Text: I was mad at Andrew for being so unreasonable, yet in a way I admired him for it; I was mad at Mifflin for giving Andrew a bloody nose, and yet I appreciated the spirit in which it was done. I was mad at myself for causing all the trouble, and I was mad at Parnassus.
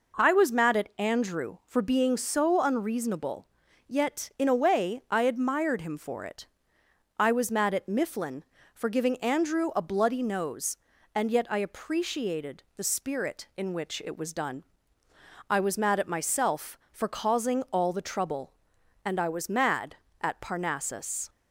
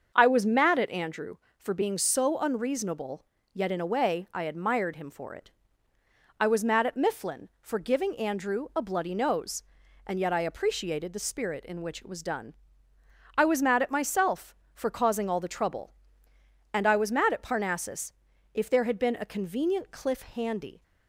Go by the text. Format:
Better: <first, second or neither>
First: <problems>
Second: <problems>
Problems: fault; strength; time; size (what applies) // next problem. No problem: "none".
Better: first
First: none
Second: starts louder than the rest; until 1.1 s; 7 dB // goes on to say "If there had been a convenient cliff handy"; strong; from 18.5 s on; 2.3 s long